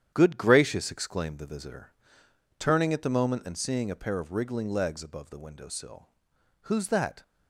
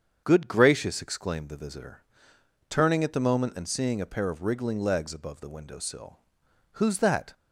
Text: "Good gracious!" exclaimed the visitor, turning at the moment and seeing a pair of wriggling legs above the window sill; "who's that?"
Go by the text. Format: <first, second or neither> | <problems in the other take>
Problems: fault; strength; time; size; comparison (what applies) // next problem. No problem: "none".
second | gets quieter; strong; throughout; 8 dB // starts louder than the rest; strong; until 1.1 s; 9.5 dB; strong in the second